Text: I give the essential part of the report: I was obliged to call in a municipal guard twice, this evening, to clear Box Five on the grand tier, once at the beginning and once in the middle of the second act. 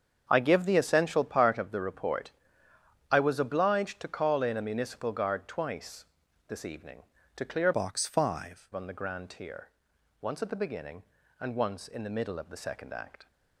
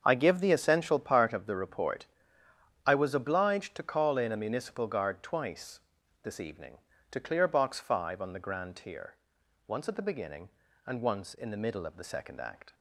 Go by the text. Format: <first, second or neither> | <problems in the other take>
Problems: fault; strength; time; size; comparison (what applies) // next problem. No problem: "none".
second | starts louder than the rest; strong; until 1.3 s; 7.5 dB; also in the second // changes voice from "Box" to "Five"; from 7.7 to 8.6 s; 0.9 s long